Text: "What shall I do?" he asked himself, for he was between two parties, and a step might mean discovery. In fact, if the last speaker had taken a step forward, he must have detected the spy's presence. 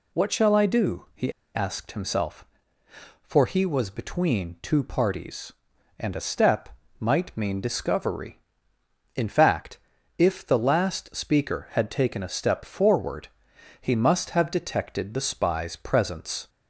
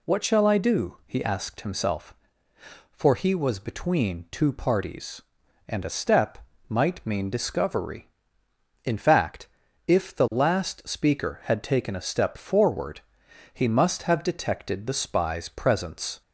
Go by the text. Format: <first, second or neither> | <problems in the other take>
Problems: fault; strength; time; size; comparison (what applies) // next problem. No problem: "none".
second | pauses between "he" and "asked"; slight; at 1.3 s; 0.22 s long // pauses between "step" and "might"; slight; at 6.7 s; 0.28 s long; slight in the second